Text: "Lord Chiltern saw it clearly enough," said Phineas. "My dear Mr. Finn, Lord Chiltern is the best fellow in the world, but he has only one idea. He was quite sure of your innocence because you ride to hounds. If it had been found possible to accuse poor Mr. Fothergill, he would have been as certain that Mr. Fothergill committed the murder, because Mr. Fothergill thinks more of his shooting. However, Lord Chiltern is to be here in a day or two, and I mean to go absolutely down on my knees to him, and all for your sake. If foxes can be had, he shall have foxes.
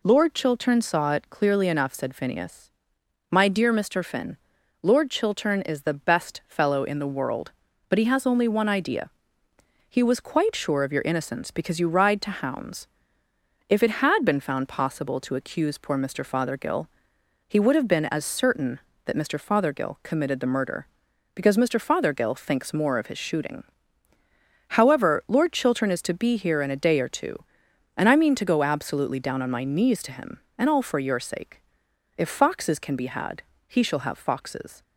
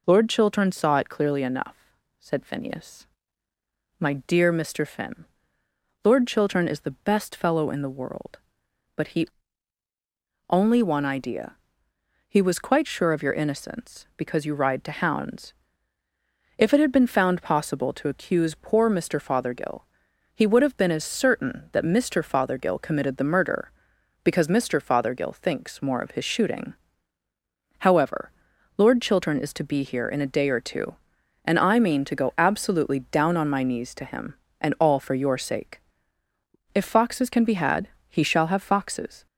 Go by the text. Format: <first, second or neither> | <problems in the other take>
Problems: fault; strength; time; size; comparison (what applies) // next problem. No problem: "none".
first | skips "has"; at 9.8 s